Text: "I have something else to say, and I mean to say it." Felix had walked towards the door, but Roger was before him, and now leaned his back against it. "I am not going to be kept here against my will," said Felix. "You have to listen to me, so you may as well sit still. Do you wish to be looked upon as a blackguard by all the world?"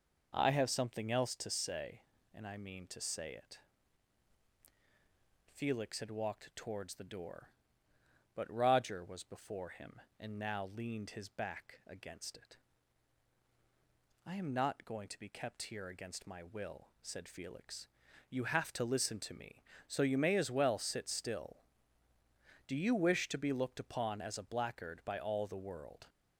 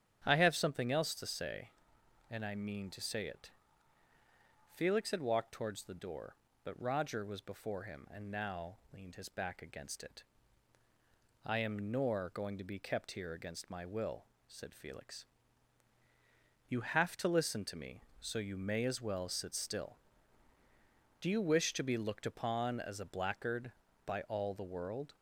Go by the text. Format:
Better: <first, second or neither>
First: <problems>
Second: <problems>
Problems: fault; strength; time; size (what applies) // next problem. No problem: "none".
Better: first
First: none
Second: starts louder than the rest; strong; until 1.2 s; 9 dB // pauses between "now" and "leaned"; slight; at 8.7 s; 0.16 s long // says "nor" for "not"; at 11.9 s